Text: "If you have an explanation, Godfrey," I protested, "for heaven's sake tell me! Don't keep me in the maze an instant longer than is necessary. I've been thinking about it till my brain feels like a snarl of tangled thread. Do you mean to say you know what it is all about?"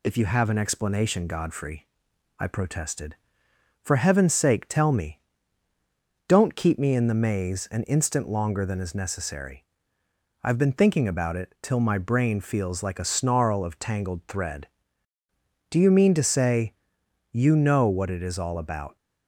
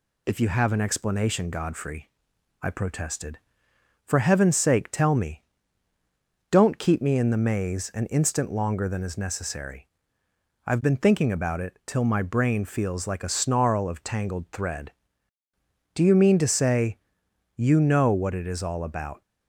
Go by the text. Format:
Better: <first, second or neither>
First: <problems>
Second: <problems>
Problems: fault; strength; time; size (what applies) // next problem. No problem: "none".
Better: neither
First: pauses between "say" and "you"; noticeable; at 16.7 s; 0.58 s long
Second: pauses between "say" and "you"; noticeable; at 16.9 s; 0.58 s long